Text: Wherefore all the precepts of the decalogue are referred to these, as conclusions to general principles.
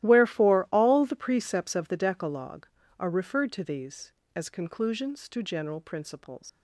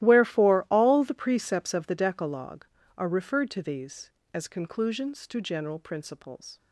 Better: second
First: starts louder than the rest; strong; until 1.0 s; 15 dB // leaves "principles" unfinished; at 6.4 s; 95 ms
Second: starts louder than the rest; strong; until 1.0 s; 15 dB

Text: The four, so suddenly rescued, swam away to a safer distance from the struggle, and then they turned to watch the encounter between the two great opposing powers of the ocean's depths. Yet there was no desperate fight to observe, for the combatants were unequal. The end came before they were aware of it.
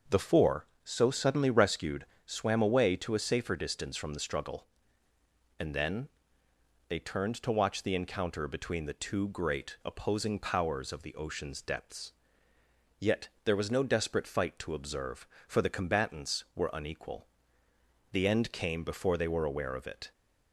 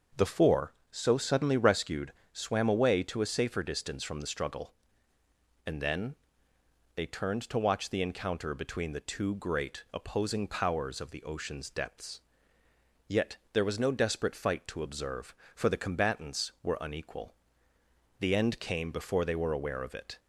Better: neither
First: starts louder than the rest; until 1.2 s; 6.5 dB // pauses between "then" and "they"; noticeable; at 6.0 s; 0.80 s long // pauses between "Yet" and "there"; slight; at 13.2 s; 0.16 s long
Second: starts louder than the rest; until 1.3 s; 6.5 dB // pauses between "then" and "they"; noticeable; at 6.1 s; 0.80 s long // pauses between "Yet" and "there"; slight; at 13.3 s; 0.16 s long

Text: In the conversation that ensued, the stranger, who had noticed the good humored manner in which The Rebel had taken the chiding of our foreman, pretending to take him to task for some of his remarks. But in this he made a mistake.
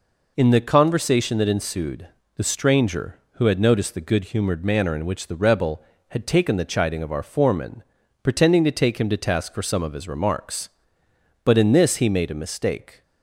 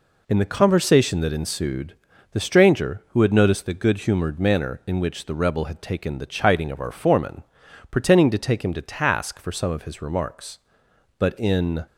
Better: first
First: none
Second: stops before "this he made a mistake"; at 11.8 s

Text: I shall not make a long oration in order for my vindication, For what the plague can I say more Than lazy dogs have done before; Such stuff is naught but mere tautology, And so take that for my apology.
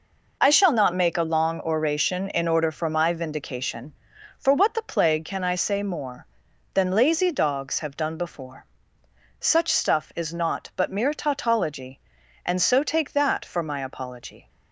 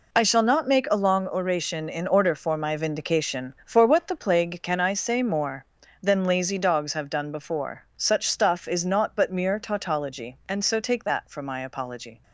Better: neither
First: none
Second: none

